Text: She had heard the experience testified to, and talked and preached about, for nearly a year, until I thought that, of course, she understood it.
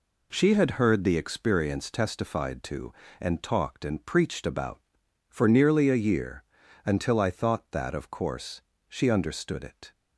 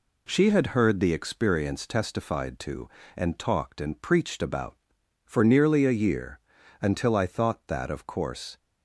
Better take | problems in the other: first | stops before "she understood it"; at 8.5 s

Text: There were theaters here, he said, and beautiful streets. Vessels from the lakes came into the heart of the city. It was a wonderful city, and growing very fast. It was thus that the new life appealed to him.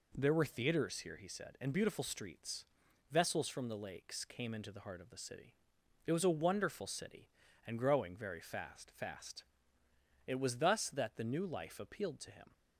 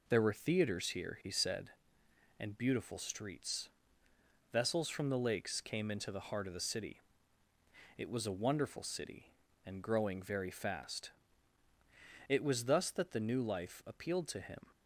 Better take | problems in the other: second | says "fast" twice; at 8.9 s

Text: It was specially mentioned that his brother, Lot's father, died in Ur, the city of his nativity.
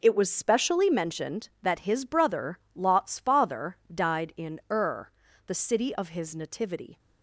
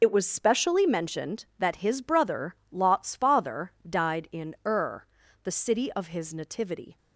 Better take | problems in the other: first | loses the start of "It"; at 0.0 s; 40 ms

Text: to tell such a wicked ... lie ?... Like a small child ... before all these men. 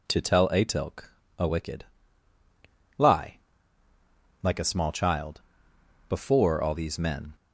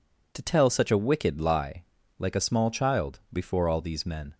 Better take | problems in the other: second | says "atilk" for "such"; at 0.4 s

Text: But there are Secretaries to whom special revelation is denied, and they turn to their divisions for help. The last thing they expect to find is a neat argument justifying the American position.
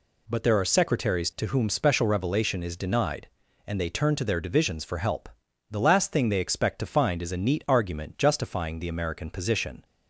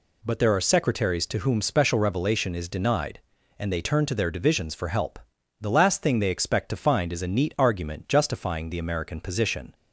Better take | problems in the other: neither | none

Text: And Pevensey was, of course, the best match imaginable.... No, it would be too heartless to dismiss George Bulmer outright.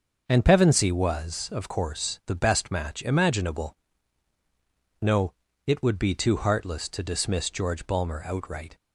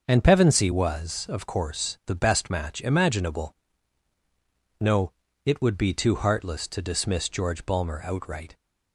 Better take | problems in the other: neither | starts louder than the rest; the same in both

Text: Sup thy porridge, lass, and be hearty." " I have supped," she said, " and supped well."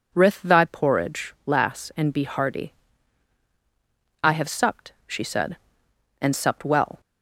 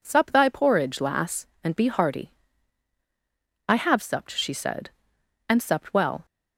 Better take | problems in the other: second | says "Rith" for "Sup"; at 0.1 s

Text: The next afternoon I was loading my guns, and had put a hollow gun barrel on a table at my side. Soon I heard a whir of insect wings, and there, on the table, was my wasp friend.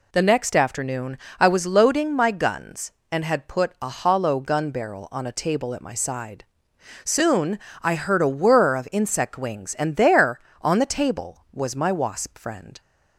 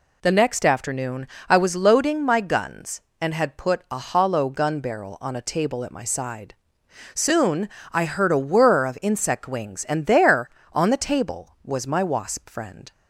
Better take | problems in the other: neither | pauses between "afternoon" and "I"; slight; the same in both // pauses between "Soon" and "I"; slight; the same in both

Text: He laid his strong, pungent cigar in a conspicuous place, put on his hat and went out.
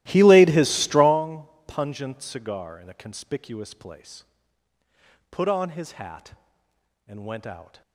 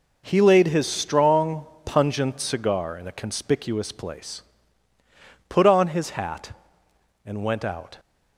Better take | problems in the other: second | starts louder than the rest; strong; until 1.2 s; 15.5 dB

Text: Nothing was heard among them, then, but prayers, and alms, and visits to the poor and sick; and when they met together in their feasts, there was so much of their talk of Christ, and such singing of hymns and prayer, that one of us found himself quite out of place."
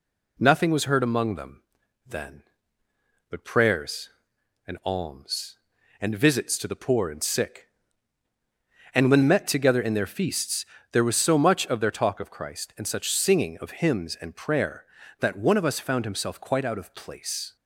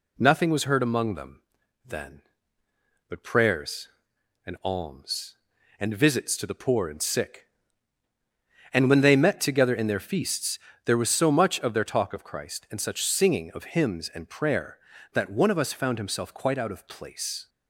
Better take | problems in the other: second | skips "they"; at 9.2 s

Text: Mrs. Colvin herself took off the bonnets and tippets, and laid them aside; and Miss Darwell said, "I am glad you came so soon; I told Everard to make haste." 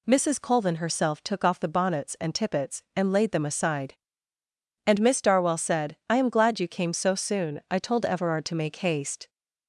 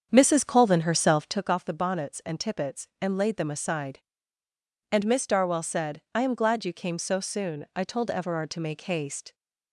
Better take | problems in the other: first | starts louder than the rest; strong; until 1.5 s; 7.5 dB

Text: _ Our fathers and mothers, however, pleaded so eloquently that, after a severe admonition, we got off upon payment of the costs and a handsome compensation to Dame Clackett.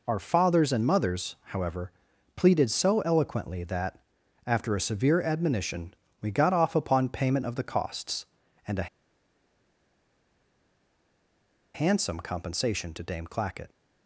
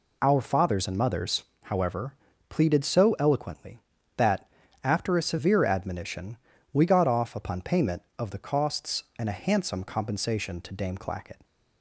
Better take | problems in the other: second | pauses between "a" and "handsome"; strong; at 8.8 s; 2.8 s long

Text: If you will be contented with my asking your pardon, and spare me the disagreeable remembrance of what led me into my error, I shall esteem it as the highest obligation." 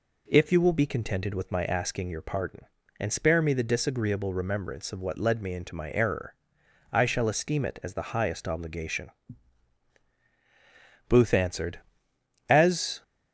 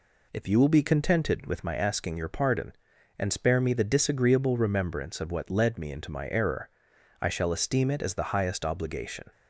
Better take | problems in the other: second | goes on to say "Booth answered As"; strong; from 11.0 s on; 1.9 s long

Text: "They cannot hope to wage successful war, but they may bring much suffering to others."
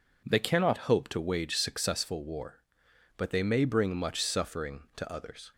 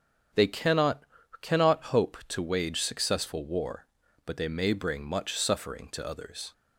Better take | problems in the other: first | starts louder than the rest; strong; until 1.7 s; 8 dB // says "cannot" twice; at 1.4 s

